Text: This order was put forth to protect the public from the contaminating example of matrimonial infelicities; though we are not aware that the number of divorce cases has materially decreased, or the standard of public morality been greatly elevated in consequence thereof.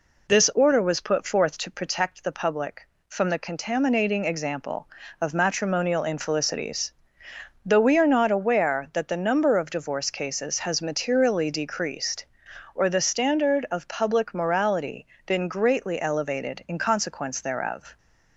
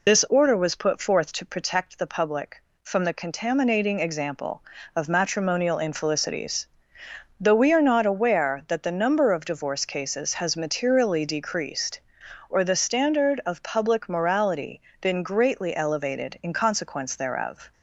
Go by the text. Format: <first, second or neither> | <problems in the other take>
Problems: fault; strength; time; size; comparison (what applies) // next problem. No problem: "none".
first | loses the start of "This"; at 0.0 s; 30 ms // pauses between "morality" and "been"; slight; at 14.7 s; 0.20 s long; slight in the first